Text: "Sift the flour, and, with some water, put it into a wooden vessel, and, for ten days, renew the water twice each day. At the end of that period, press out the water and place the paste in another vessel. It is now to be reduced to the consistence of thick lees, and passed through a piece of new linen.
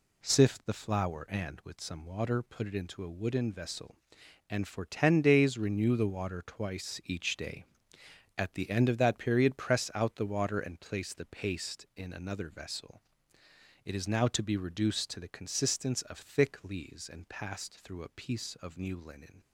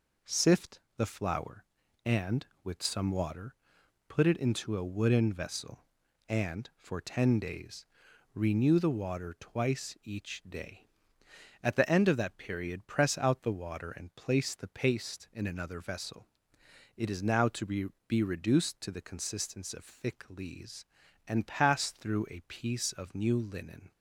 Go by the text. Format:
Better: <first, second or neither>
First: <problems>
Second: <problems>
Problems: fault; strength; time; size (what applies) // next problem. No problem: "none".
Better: first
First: none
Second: pauses between "Sift" and "the"; slight; at 0.7 s; 0.16 s long // says "be" twice; at 18.0 s